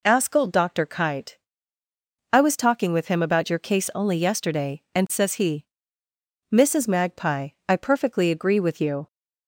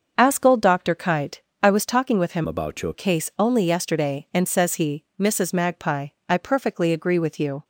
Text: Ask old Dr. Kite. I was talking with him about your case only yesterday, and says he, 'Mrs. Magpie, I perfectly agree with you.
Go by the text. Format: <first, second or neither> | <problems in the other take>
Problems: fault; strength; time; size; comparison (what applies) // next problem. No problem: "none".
first | starts louder than the rest; until 1.2 s; 6 dB // changes voice from "about" to "your"; from 2.4 to 2.9 s; 0.5 s long